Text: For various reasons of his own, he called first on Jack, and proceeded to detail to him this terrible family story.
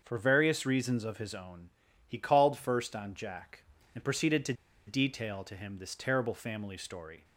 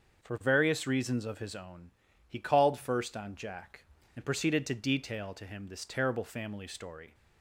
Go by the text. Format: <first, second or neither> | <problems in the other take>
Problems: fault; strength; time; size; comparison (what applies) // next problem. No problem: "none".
second | starts louder than the rest; until 1.0 s; 6.5 dB; also in the second // pauses between "to" and "detail"; slight; at 4.5 s; 0.33 s long